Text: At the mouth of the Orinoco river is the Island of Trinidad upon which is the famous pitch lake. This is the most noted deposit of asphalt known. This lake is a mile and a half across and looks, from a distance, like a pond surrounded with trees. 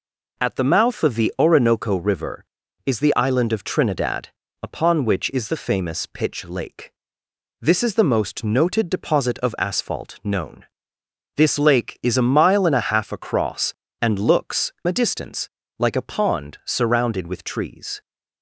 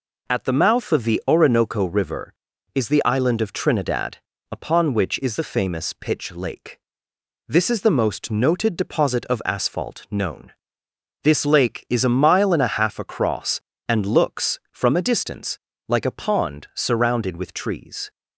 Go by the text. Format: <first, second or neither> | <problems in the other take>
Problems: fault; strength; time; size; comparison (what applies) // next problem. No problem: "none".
second | pauses between "Trinidad" and "upon"; slight; at 4.2 s; 0.32 s long; slight in the second // skips "from"; at 14.7 s